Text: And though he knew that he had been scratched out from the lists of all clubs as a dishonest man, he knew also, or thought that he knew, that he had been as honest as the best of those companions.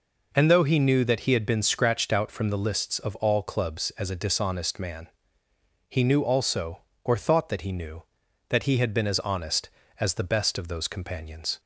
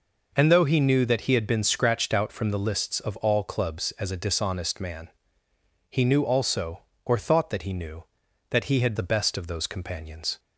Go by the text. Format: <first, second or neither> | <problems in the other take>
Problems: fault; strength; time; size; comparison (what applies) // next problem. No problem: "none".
first | skips "been as honest as"; at 8.9 s